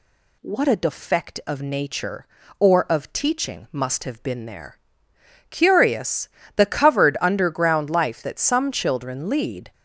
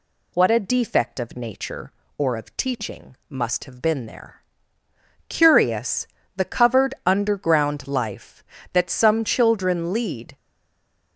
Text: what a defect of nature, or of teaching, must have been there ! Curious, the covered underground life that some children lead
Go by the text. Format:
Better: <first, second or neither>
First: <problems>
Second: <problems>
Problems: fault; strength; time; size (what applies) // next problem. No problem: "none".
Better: first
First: none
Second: stays silent after the last word; slight; from 10.3 s on; 0.8 s long